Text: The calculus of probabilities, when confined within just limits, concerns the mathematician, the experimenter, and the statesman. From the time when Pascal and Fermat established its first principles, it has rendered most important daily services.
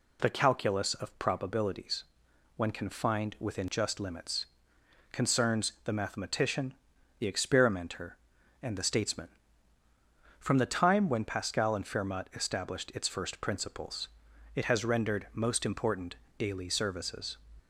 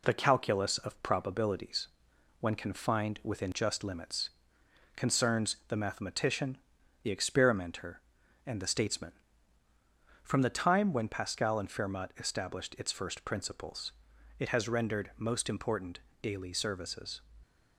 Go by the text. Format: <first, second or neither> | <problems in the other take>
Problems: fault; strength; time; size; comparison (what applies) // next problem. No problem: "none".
first | gets quieter; slight; throughout; 3 dB // pauses between "important" and "daily"; slight; at 16.0 s; 0.20 s long; slight in the first